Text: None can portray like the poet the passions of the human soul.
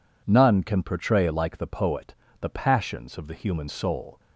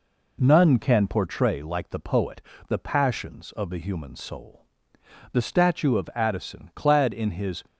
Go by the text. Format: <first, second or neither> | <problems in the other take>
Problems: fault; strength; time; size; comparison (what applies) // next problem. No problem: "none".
first | pauses between "poet" and "the"; slight; at 2.4 s; 0.28 s long; slight in the first // goes on to say "The statue of Addison clad in his"; strong; from 5.3 s on; 2.3 s long